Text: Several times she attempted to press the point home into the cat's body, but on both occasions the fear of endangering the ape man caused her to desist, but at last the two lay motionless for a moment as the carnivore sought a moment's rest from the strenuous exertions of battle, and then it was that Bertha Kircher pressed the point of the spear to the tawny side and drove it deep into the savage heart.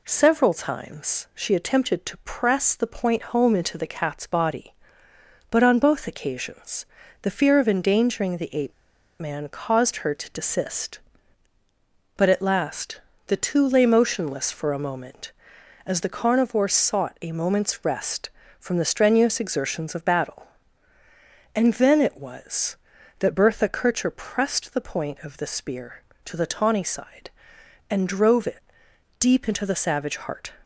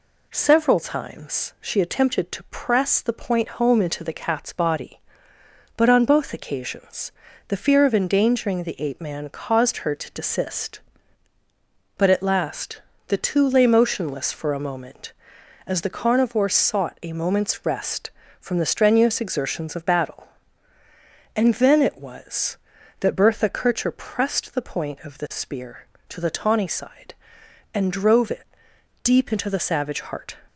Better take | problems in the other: second | pauses between "occasions" and "the"; slight; at 6.8 s; 0.36 s long; slight in the second // pauses between "ape" and "man"; noticeable; at 8.7 s; 0.47 s long // pauses between "last" and "the"; slight; at 12.9 s; 0.28 s long; slight in the second // pauses between "it" and "deep"; noticeable; at 28.6 s; 0.58 s long; noticeable in the second

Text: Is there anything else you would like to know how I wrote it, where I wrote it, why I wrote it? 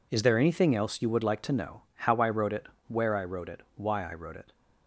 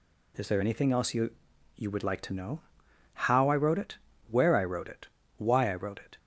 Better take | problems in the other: first | says "you" twice; at 1.7 s // pauses between "know" and "how"; noticeable; at 2.6 s; 0.52 s long

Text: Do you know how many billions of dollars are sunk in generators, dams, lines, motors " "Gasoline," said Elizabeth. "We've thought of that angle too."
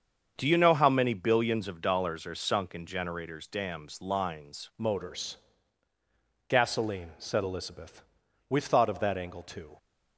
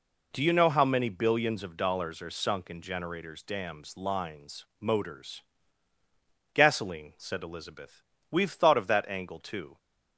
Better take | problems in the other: second | starts louder than the rest; strong; until 1.3 s; 7.5 dB // changes voice at "motors"; from 4.7 s on; 5.0 s long

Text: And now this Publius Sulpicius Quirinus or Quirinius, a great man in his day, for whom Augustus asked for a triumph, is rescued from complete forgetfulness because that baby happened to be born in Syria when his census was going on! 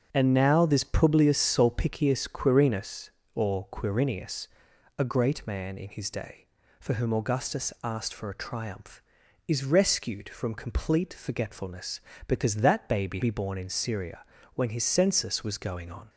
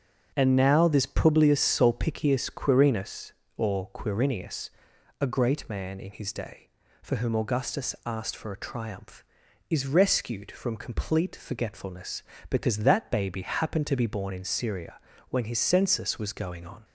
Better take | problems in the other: second | starts louder than the rest; until 1.1 s; 6.5 dB; also in the second // skips "happened to"; at 13.2 s // pauses between "Syria" and "when"; slight; at 14.2 s; 0.30 s long; slight in the second

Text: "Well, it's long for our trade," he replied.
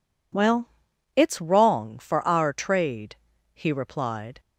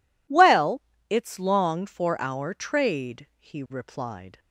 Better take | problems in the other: second | says "wrong" for "long"; at 1.3 s

